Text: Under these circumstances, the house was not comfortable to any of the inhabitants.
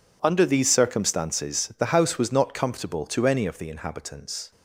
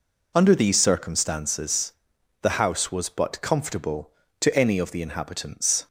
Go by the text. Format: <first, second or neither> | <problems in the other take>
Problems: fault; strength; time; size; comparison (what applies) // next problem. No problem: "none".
first | says "but" for "not"; at 3.0 s